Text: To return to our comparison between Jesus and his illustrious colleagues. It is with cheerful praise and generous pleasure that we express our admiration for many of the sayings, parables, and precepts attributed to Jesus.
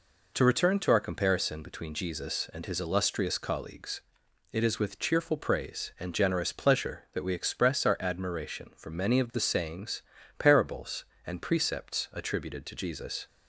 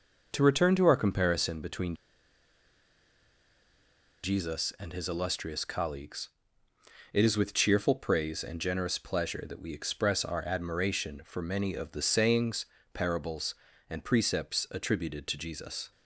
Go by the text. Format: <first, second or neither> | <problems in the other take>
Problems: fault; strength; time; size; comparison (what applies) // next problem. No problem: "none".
first | pauses between "between" and "Jesus"; strong; at 1.9 s; 2.2 s long